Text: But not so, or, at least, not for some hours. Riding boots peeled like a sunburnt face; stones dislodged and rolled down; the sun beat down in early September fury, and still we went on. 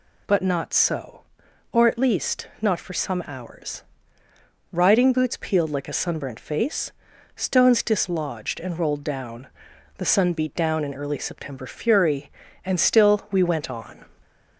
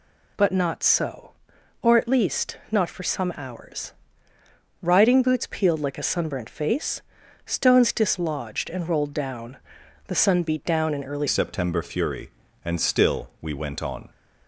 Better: first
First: none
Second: changes voice at "September"; from 11.2 s on; 2.8 s long

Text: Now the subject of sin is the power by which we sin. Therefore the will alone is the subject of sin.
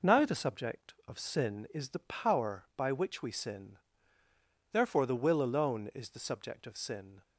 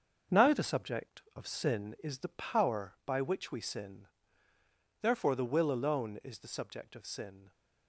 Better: first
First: none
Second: gets quieter; noticeable; throughout; 6 dB

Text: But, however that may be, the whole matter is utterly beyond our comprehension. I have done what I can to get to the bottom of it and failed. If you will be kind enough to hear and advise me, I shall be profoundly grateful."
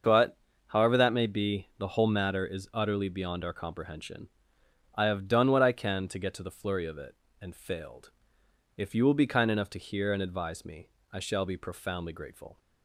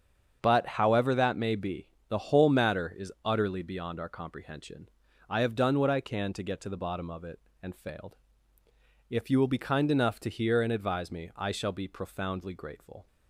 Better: second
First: starts louder than the rest; until 1.3 s; 6.5 dB // says "flurry" for "bottom"; at 6.5 s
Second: starts louder than the rest; strong; until 1.4 s; 7.5 dB

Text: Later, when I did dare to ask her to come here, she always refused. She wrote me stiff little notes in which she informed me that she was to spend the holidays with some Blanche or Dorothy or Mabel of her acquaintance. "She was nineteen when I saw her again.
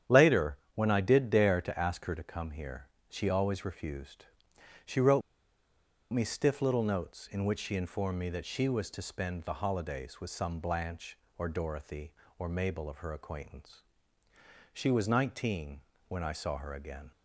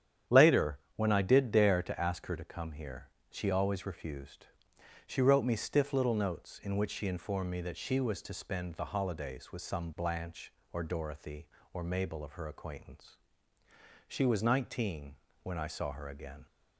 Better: second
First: starts louder than the rest; strong; until 1.2 s; 9.5 dB // pauses between "wrote" and "me"; noticeable; at 5.2 s; 0.91 s long // pauses between "nineteen" and "when"; slight; at 15.7 s; 0.30 s long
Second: starts louder than the rest; strong; until 1.4 s; 9.5 dB // pauses between "nineteen" and "when"; slight; at 15.1 s; 0.30 s long

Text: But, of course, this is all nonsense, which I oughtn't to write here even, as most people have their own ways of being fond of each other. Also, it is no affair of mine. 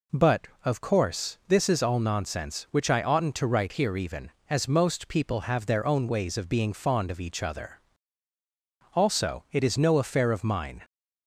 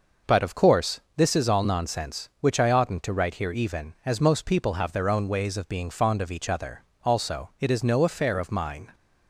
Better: neither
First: none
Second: none

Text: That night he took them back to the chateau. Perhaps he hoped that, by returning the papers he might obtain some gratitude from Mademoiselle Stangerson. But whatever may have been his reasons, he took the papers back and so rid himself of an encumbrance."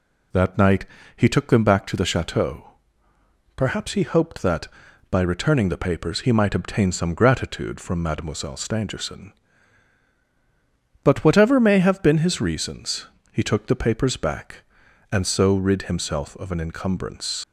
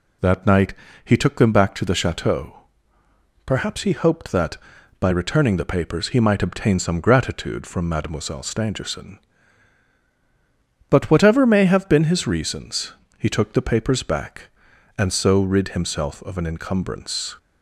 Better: second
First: pauses between "night" and "he"; slight; at 0.8 s; 0.30 s long // leaves "encumbrance" unfinished; at 17.4 s; 75 ms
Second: pauses between "night" and "he"; slight; at 0.7 s; 0.30 s long

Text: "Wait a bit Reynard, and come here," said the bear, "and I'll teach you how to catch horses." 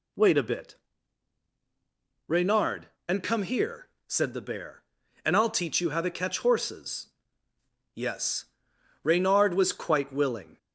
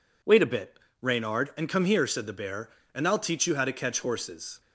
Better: second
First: pauses between "bit" and "Reynard"; strong; at 0.7 s; 1.5 s long // goes on to say "Yes Reynard was quite willing"; strong; from 7.9 s on; 2.6 s long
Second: pauses between "bit" and "Reynard"; slight; at 0.7 s; 0.22 s long

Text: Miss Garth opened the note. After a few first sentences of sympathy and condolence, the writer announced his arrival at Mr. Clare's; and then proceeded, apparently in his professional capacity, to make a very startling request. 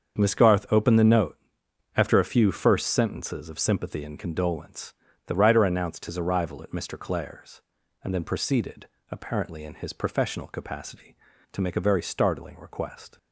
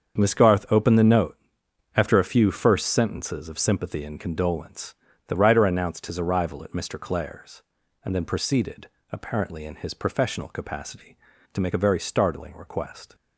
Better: neither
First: starts louder than the rest; until 1.2 s; 7 dB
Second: starts louder than the rest; until 1.2 s; 7 dB

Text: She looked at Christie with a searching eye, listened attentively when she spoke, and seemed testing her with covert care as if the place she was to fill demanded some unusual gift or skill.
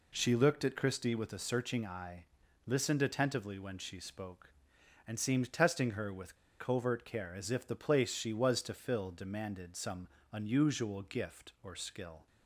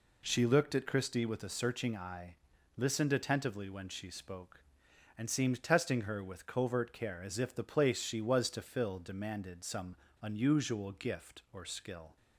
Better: second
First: pauses between "with" and "covert"; slight; at 6.3 s; 0.23 s long // pauses between "some" and "unusual"; slight; at 10.0 s; 0.24 s long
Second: pauses between "some" and "unusual"; slight; at 9.9 s; 0.25 s long

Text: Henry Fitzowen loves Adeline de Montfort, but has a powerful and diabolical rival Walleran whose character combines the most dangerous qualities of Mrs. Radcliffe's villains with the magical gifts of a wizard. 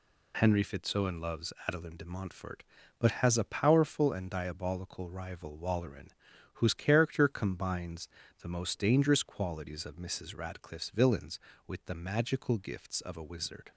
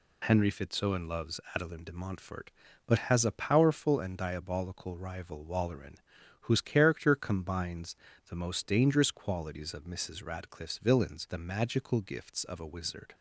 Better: first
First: pauses between "Walleran" and "whose"; noticeable; at 6.0 s; 0.46 s long // pauses between "combines" and "the"; slight; at 8.0 s; 0.32 s long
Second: pauses between "Walleran" and "whose"; noticeable; at 5.9 s; 0.46 s long // pauses between "combines" and "the"; slight; at 7.9 s; 0.32 s long // skips "with"; at 11.2 s

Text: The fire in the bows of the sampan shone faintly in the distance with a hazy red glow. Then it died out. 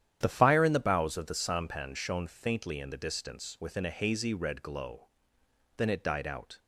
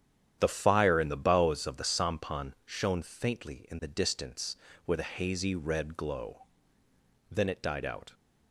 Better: second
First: starts louder than the rest; strong; until 1.2 s; 10.5 dB // says "within" for "with"; at 3.6 s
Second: starts louder than the rest; strong; until 1.4 s; 10 dB

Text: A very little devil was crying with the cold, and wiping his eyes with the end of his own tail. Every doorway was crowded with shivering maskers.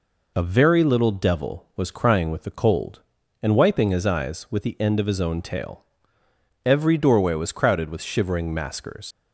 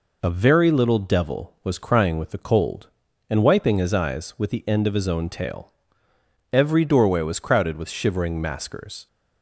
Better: second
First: leaves "maskers" unfinished; at 9.1 s; 85 ms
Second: none

